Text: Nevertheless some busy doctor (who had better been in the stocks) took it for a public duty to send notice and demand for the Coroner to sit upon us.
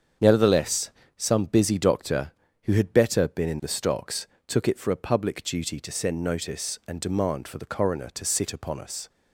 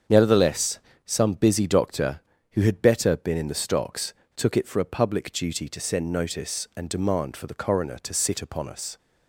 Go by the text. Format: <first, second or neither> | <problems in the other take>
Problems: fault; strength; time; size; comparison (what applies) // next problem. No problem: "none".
neither | starts louder than the rest; strong; the same in both // pauses between "Nevertheless" and "some"; slight; the same in both